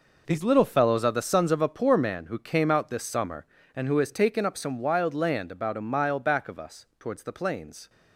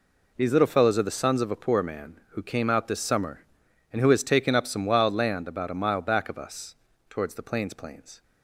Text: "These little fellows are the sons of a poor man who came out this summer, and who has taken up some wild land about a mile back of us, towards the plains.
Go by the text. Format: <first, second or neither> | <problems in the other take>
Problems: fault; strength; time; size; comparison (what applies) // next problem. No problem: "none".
first | says "plains" twice; at 7.7 s